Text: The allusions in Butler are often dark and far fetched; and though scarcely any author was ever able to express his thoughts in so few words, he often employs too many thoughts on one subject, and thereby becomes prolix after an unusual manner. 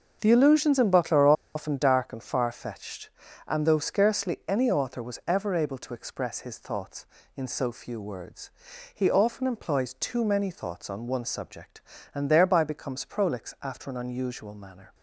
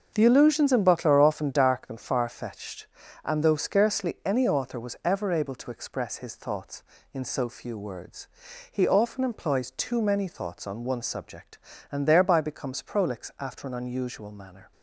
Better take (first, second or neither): second